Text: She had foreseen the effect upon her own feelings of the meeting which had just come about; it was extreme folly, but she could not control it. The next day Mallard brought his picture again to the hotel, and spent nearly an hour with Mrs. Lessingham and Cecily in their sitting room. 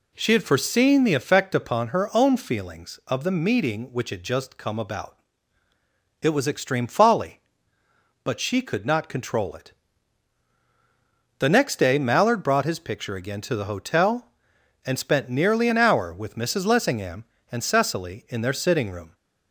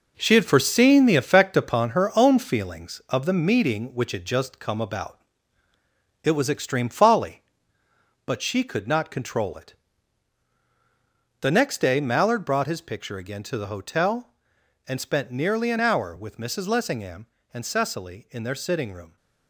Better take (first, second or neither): first